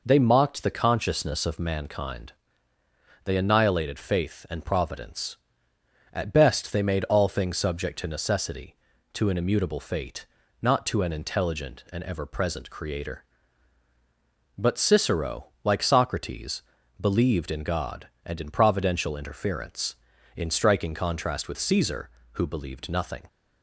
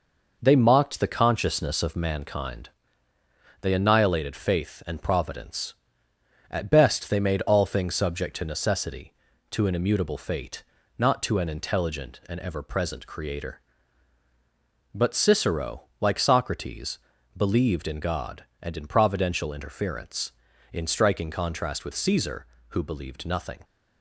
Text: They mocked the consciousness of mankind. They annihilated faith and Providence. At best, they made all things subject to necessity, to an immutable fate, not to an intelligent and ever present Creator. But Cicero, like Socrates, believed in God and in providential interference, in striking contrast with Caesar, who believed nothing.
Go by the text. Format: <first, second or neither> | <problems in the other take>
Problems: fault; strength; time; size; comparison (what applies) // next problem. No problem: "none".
first | gets quieter; noticeable; throughout; 4.5 dB